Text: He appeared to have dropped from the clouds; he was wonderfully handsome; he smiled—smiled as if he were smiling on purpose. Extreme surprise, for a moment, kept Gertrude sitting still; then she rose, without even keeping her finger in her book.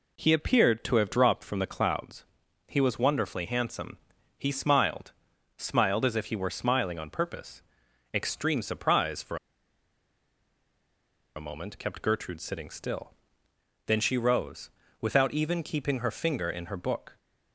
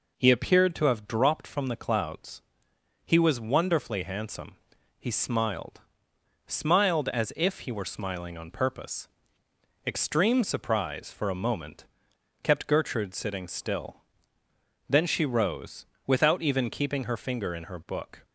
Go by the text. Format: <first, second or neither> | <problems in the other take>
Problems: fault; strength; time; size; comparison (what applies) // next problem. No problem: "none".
second | pauses between "for" and "a"; strong; at 9.3 s; 2.0 s long